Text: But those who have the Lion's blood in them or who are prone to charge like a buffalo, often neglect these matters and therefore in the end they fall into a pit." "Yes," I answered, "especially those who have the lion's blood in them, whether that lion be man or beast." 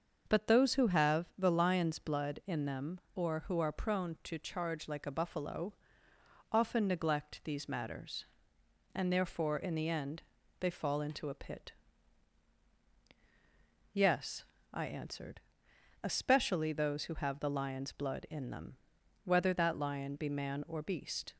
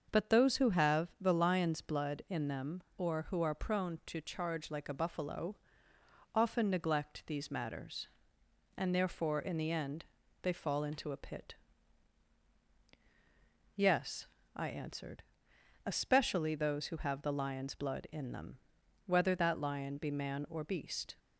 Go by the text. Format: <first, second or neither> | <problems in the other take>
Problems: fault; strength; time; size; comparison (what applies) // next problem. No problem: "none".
neither | starts louder than the rest; the same in both // pauses between "end" and "they"; the same in both